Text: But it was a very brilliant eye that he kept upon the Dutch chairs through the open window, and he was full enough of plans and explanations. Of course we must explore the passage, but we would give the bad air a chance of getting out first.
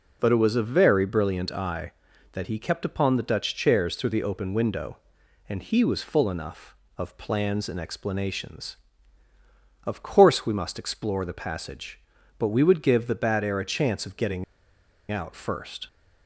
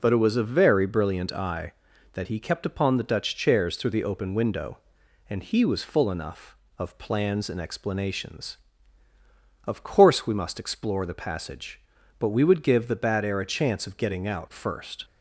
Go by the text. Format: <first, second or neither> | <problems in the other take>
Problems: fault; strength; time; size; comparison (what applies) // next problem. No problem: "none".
second | pauses between "getting" and "out"; noticeable; at 14.4 s; 0.67 s long